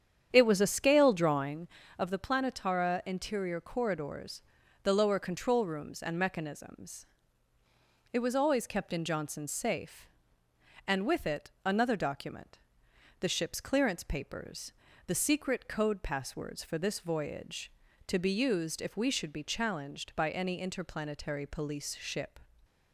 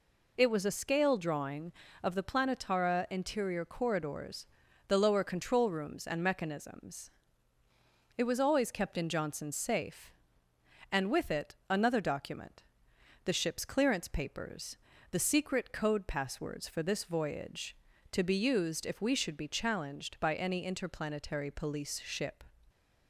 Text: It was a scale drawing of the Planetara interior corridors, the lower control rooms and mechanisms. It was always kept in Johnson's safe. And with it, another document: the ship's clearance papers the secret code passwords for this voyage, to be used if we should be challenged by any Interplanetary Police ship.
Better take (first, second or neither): second